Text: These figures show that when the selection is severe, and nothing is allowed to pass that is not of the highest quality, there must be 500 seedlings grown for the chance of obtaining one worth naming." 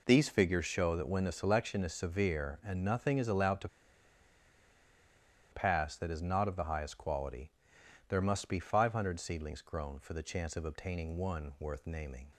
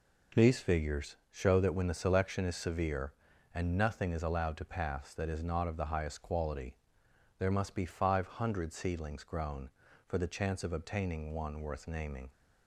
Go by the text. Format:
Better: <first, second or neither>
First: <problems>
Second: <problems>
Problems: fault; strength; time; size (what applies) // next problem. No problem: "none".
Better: second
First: pauses between "to" and "pass"; strong; at 3.6 s; 1.8 s long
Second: none